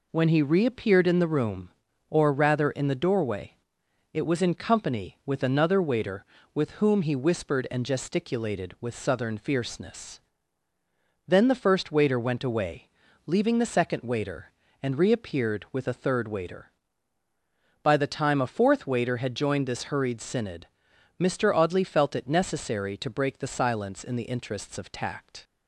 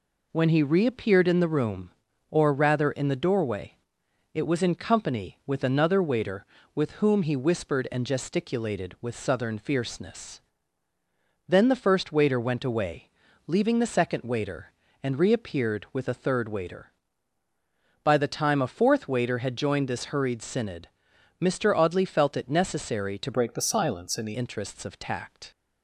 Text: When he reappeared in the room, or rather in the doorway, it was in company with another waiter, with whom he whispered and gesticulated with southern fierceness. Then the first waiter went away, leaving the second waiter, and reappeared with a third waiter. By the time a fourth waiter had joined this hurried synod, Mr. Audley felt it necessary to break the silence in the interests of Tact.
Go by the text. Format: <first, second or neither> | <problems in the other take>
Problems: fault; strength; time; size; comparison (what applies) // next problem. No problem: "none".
first | changes voice from "break" to "the"; from 23.3 to 24.3 s; 1.0 s long